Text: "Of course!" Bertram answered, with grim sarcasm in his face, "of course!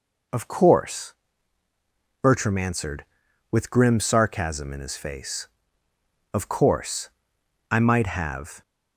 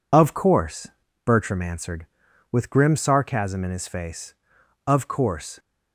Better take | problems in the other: second | goes on to say "I might have"; noticeable; from 7.6 s on; 0.92 s long

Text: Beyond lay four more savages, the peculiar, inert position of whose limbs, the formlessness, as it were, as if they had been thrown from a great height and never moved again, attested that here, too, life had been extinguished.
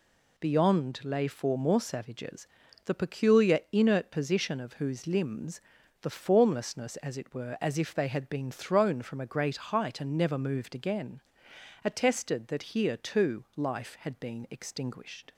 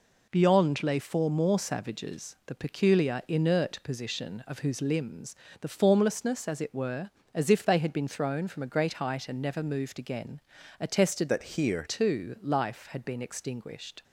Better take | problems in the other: first | changes voice from "that" to "here"; from 11.2 to 11.8 s; 0.6 s long

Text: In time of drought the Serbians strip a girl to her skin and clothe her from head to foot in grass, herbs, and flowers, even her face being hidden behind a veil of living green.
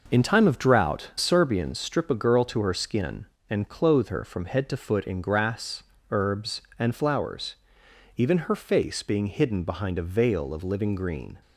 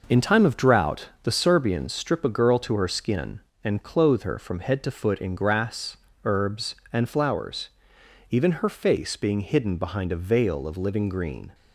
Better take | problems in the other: second | skips "the"; at 1.1 s

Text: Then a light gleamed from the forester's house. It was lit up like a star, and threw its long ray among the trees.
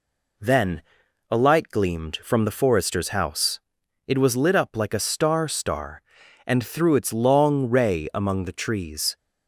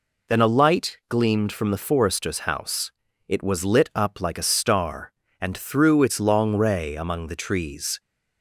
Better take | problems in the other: second | pauses between "Then" and "a"; noticeable; at 0.8 s; 0.48 s long // says "star" twice; at 5.4 s

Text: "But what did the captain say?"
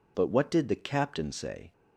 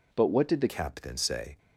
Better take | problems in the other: first | changes voice at "captain"; from 0.6 s on; 0.9 s long

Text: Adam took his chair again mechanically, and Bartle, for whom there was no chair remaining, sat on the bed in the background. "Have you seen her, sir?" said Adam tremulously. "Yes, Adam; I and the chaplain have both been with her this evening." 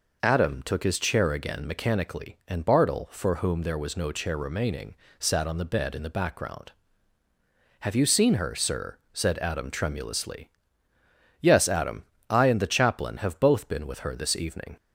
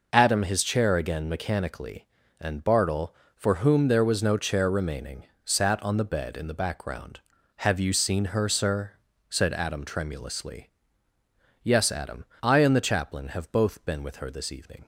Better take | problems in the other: first | skips "took"; at 0.4 s

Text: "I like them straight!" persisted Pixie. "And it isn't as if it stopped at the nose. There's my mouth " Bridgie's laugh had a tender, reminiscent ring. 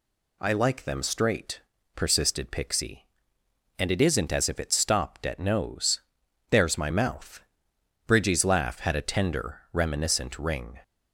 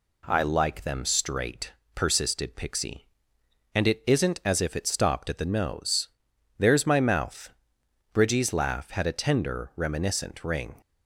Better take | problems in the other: second | skips "the"; at 5.4 s

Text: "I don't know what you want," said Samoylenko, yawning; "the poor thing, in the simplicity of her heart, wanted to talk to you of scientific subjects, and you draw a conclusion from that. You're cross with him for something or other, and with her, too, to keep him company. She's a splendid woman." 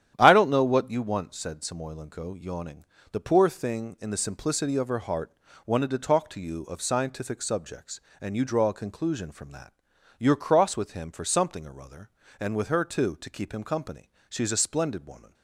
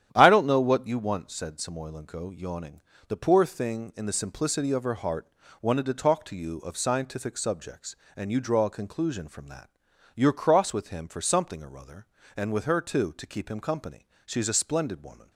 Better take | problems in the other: neither | starts louder than the rest; strong; the same in both

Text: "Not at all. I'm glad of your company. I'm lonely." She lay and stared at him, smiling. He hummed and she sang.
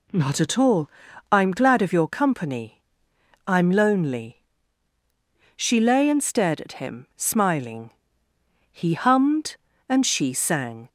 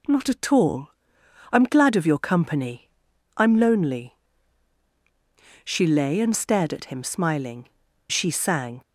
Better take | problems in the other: first | skips "He hummed and"; at 7.8 s

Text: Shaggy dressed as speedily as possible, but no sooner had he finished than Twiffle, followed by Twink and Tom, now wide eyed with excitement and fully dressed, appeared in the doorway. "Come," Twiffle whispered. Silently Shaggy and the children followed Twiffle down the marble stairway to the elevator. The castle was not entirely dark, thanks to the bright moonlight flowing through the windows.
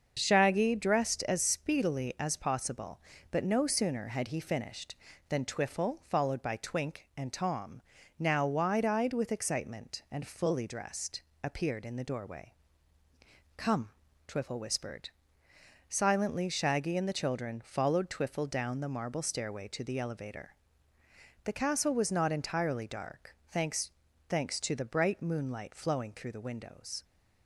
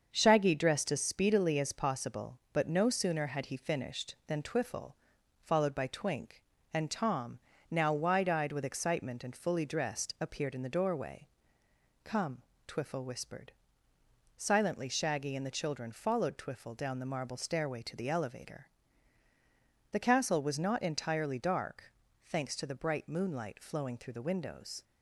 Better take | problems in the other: second | starts louder than the rest; until 1.1 s; 6.5 dB; also in the second // says "thanks" twice; at 24.2 s

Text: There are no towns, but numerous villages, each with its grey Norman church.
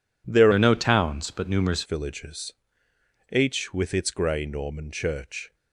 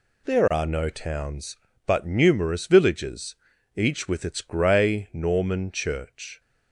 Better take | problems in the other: second | changes voice from "are" to "numerous"; from 0.5 to 1.8 s; 1.3 s long

